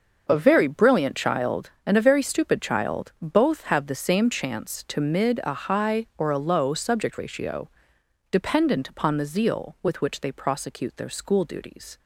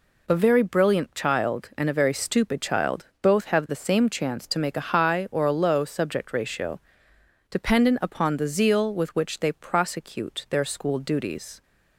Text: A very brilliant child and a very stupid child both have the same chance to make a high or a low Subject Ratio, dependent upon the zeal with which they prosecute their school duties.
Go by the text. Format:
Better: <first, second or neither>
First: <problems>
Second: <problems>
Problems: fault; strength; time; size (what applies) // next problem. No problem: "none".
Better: second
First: starts louder than the rest; until 1.3 s; 6.5 dB // says "mid" for "make"; at 4.9 s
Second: none